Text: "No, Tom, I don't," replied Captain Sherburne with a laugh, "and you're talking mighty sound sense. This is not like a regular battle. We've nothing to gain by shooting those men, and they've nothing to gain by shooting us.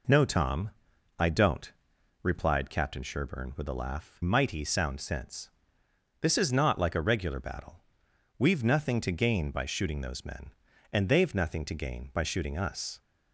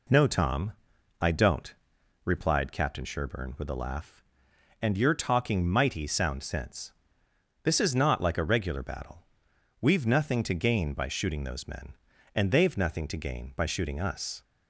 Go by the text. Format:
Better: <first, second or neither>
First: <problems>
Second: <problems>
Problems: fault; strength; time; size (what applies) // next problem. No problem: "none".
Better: second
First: skips "and you're talking"; at 4.2 s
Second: none